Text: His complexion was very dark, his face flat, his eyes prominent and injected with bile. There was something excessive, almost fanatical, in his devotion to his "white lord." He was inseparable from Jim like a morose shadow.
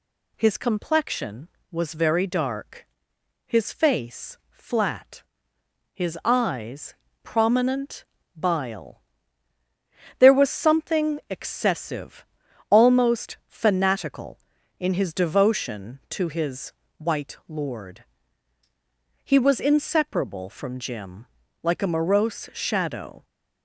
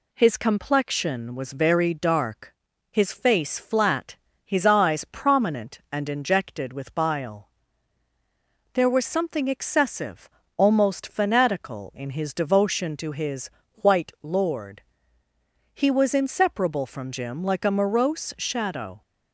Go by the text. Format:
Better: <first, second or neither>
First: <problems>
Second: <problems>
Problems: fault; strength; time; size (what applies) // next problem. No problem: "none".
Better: second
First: pauses between "eyes" and "prominent"; slight; at 6.9 s; 0.28 s long // skips "and injected with"; at 8.2 s // pauses between "his" and "white"; slight; at 16.7 s; 0.26 s long // pauses between "Jim" and "like"; slight; at 21.2 s; 0.36 s long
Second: pauses between "his" and "white"; slight; at 13.4 s; 0.26 s long